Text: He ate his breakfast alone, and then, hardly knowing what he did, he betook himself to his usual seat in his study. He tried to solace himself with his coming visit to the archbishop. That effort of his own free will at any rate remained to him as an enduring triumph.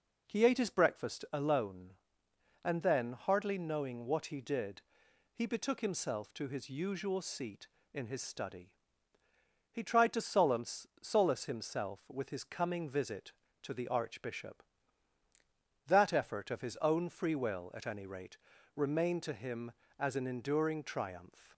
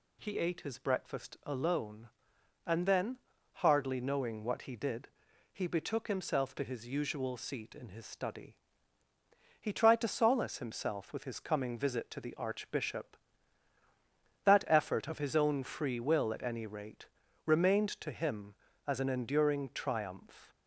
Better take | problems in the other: second | says "solace" twice; at 11.0 s // pauses between "rate" and "remained"; slight; at 18.3 s; 0.36 s long; also in the second

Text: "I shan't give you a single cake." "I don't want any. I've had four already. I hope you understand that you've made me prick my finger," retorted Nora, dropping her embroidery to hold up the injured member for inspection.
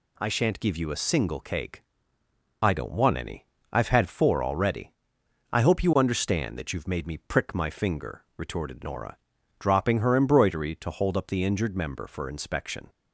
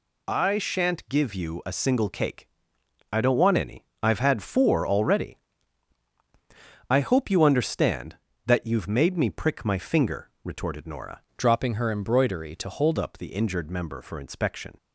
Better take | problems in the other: first | changes voice from "dropping" to "hold"; from 11.3 to 12.9 s; 1.6 s long

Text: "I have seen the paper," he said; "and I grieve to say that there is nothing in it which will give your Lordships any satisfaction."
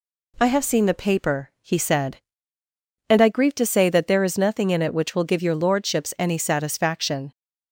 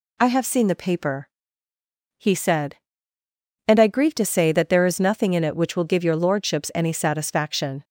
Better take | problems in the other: neither | none

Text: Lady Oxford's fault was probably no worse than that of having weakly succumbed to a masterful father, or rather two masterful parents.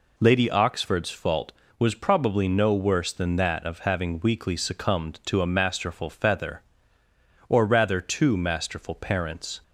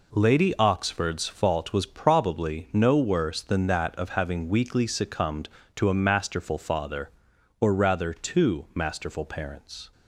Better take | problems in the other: second | says "feather" for "father"; at 6.0 s

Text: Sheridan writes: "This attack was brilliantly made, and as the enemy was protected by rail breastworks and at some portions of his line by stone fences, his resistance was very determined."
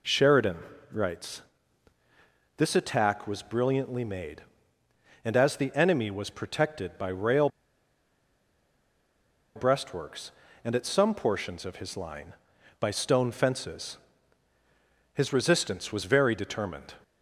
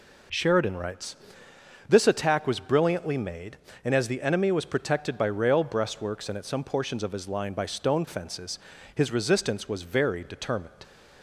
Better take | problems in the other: second | pauses between "Sheridan" and "writes"; slight; at 0.5 s; 0.32 s long // pauses between "rail" and "breastworks"; strong; at 7.4 s; 2.0 s long

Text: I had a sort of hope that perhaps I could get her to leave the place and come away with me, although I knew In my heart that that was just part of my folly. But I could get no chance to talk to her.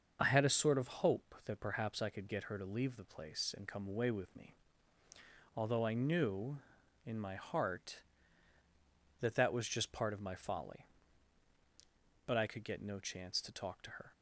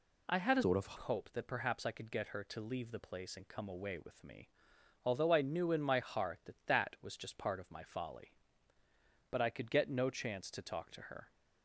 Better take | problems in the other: first | changes voice from "sort" to "of"; from 0.6 to 0.9 s; 0.3 s long

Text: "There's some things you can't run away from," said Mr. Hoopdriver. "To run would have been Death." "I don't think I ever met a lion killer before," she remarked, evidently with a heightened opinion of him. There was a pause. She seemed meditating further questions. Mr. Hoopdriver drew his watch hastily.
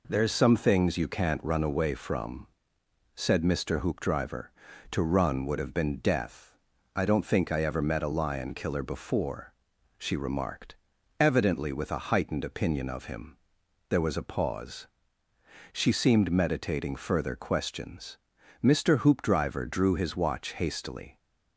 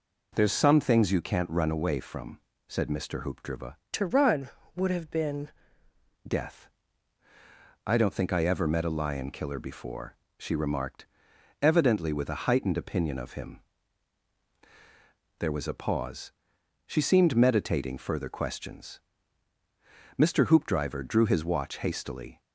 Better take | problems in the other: first | changes voice from "To" to "been"; from 3.9 to 5.4 s; 1.5 s long

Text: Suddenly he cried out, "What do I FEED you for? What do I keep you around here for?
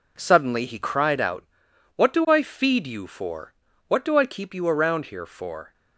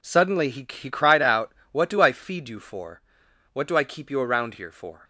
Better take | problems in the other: first | says "he" twice; at 0.6 s

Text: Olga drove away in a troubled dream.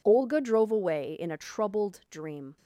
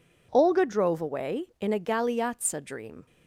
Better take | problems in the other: first | says "galeazza" for "troubled"; at 1.7 s

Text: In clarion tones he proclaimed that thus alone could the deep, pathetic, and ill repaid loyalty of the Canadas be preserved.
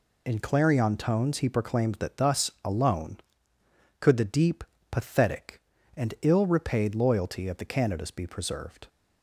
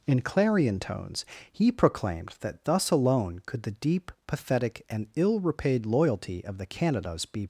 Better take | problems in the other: first | pauses between "tones" and "he"; slight; at 1.2 s; 0.24 s long // stops before "preserved"; at 7.4 s

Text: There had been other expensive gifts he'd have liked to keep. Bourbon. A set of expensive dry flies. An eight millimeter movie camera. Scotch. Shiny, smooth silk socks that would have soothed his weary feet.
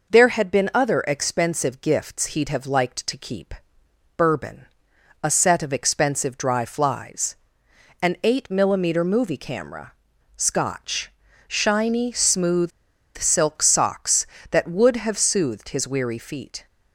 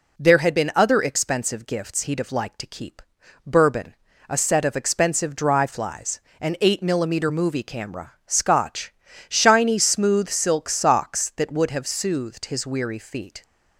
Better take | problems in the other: second | pauses between "smooth" and "silk"; noticeable; at 12.7 s; 0.47 s long

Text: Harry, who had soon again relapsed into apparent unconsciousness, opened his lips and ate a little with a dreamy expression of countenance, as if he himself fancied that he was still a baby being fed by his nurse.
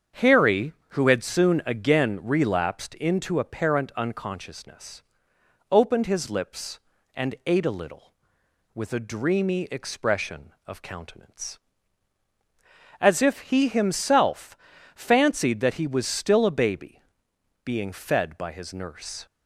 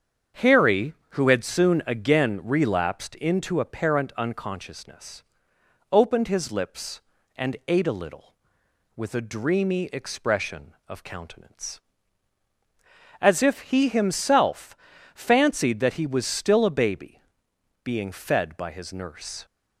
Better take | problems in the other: neither | starts louder than the rest; strong; the same in both // pauses between "himself" and "fancied"; the same in both // pauses between "baby" and "being"; noticeable; the same in both

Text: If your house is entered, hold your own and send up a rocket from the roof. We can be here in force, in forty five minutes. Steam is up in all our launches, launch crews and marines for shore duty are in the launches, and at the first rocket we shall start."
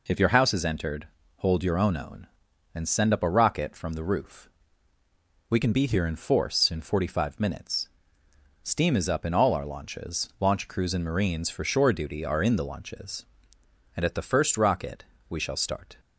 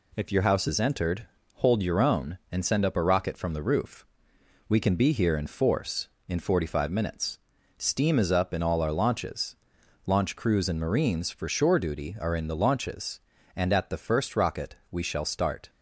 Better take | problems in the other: second | says "own" twice; at 1.9 s // pauses between "rocket" and "we"; slight; at 15.0 s; 0.24 s long; slight in the second

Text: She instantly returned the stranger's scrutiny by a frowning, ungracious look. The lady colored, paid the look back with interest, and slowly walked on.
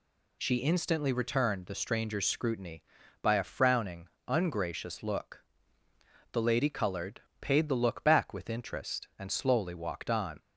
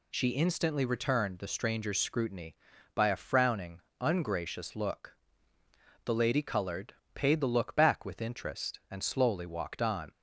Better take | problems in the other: neither | none

